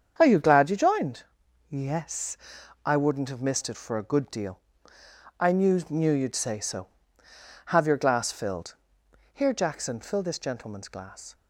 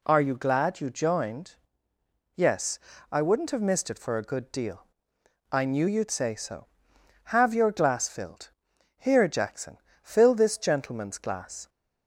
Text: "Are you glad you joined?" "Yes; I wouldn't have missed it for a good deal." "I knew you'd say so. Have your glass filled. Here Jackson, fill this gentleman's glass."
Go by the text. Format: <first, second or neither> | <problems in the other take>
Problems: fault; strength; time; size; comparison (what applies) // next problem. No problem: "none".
second | starts louder than the rest; strong; until 1.1 s; 7.5 dB // says "knew" twice; at 5.8 s